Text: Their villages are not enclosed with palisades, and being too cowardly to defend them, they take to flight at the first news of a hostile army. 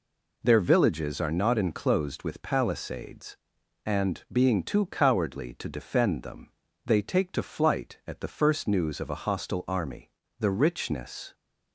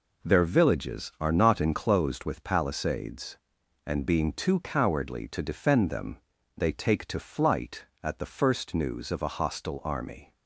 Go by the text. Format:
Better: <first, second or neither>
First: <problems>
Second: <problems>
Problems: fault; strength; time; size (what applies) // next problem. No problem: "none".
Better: second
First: goes on to say "The richness"; noticeable; from 10.3 s on; 0.96 s long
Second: none